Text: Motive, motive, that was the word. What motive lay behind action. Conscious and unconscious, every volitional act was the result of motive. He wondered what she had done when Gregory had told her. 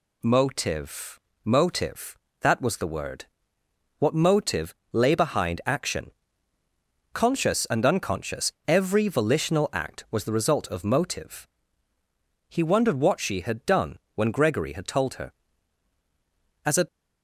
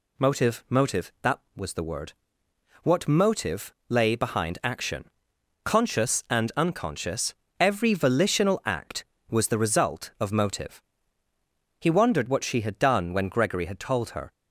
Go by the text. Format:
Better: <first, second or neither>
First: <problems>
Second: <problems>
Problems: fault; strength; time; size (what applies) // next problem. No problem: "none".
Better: second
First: pauses between "motive" and "lay"; slight; at 4.7 s; 0.18 s long // pauses between "done" and "when"; slight; at 13.9 s; 0.16 s long // goes on to say "As a"; slight; from 16.6 s on; 0.22 s long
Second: pauses between "motive" and "lay"; slight; at 3.7 s; 0.16 s long